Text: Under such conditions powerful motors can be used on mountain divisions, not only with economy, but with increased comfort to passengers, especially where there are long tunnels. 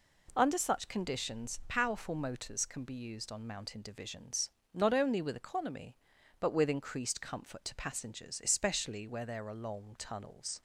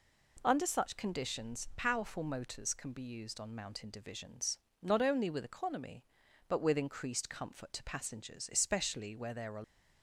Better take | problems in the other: first | stops before "long tunnels"; at 9.6 s

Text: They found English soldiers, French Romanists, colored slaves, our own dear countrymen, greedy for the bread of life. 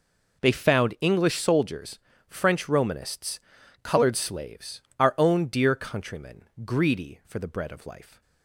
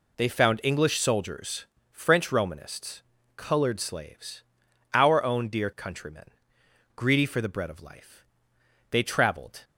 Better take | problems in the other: first | goes on to say "They traveled"; noticeable; from 8.8 s on; 0.74 s long

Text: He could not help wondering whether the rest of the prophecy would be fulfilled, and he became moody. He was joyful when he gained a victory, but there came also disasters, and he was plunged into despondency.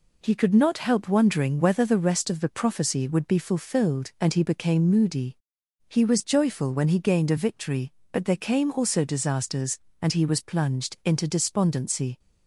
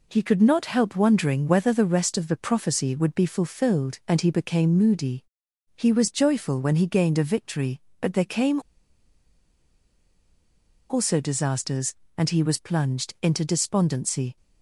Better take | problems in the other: first | pauses between "came" and "also"; strong; at 8.5 s; 2.3 s long

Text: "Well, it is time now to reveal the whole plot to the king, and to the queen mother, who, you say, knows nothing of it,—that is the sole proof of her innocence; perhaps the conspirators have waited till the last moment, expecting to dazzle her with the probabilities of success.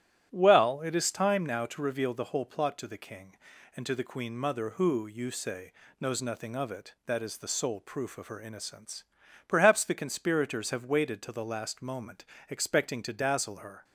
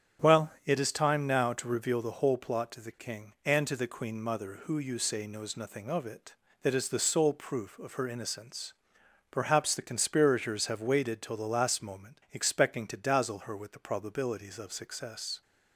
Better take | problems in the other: second | starts louder than the rest; strong; until 1.3 s; 12 dB; strong in the second // stops before "with the probabilities of success"; at 13.8 s

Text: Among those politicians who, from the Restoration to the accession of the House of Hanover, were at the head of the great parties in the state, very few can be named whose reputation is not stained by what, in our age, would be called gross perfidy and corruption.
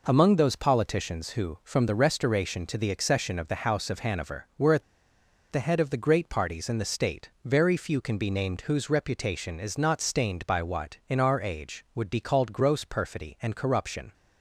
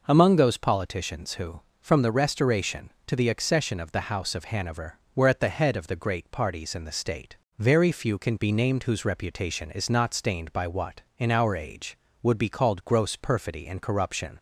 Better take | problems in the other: second | pauses between "at" and "the"; noticeable; at 4.8 s; 0.68 s long

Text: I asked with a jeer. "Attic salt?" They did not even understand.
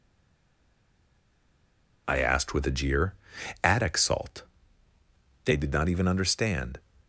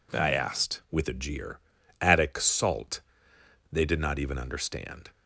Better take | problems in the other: second | stays silent before the first word; noticeable; until 2.0 s; 2.0 s long

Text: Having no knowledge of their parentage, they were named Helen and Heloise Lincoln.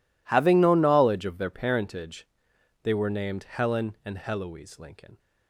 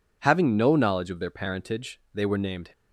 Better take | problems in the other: first | stops before "Helen and Heloise Lincoln"; at 2.7 s

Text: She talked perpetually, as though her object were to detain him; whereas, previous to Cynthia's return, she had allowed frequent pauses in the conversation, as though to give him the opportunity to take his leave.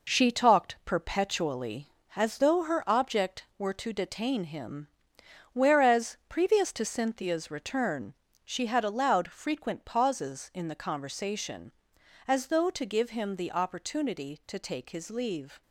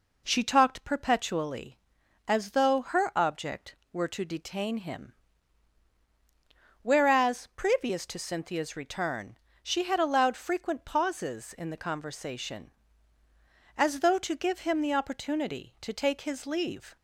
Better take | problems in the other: second | gets quieter; throughout; 6.5 dB

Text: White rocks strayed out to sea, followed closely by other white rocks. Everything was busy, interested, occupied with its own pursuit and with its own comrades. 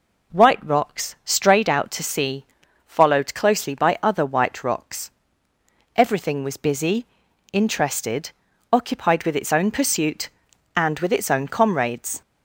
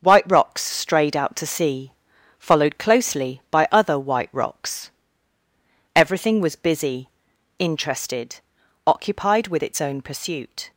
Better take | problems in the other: first | stops before "and with its own comrades"; at 10.7 s

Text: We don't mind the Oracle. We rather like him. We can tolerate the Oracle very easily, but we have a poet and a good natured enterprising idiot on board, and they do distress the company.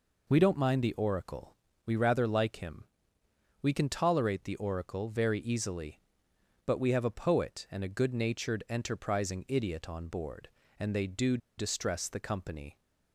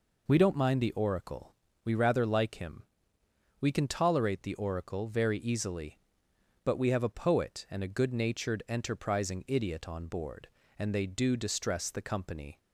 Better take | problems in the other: second | pauses between "do" and "distress"; slight; at 11.3 s; 0.20 s long

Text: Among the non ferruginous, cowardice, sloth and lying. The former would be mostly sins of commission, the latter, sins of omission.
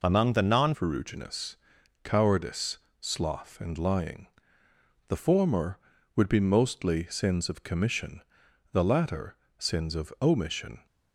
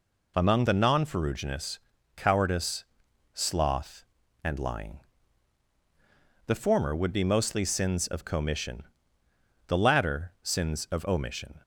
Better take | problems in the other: second | changes voice at "ferruginous"; from 0.7 s on; 10.1 s long

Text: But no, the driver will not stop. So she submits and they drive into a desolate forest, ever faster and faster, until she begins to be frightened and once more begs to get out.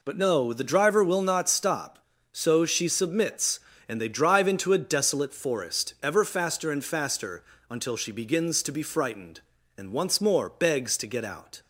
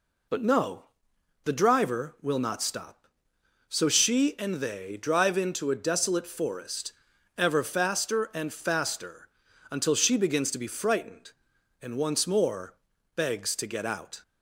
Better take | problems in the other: first | skips "submits"; at 4.3 s // pauses between "more" and "begs"; at 12.7 s; 0.42 s long

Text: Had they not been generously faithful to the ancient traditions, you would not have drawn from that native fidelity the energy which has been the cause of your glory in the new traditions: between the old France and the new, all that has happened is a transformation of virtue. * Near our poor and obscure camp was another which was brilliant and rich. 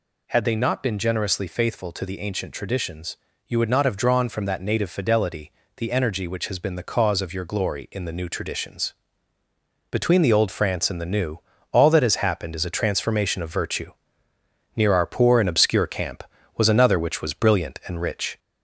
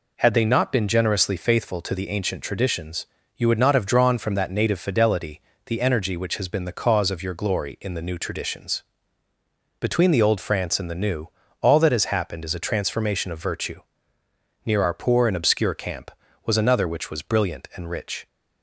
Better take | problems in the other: second | gets louder; slight; throughout; 2.5 dB // pauses between "fidelity" and "the"; slight; at 5.5 s; 0.26 s long; slight in the second

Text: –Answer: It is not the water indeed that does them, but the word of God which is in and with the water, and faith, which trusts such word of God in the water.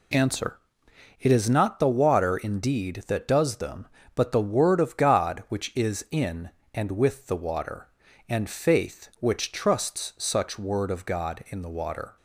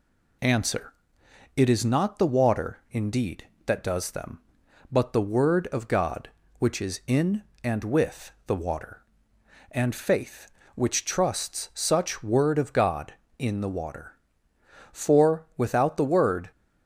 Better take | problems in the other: first | pauses between "with" and "the"; slight; at 8.3 s; 0.16 s long // goes on to say "For without the word"; from 14.9 s on; 1.5 s long

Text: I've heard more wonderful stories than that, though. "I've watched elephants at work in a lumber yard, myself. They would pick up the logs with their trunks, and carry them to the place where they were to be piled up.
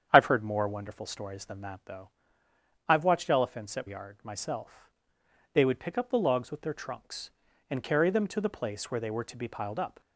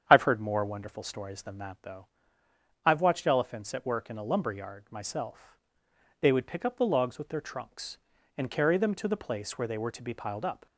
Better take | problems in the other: second | starts louder than the rest; strong; until 1.1 s; 8.5 dB; strong in the second // skips "work in a lumber"; at 3.8 s

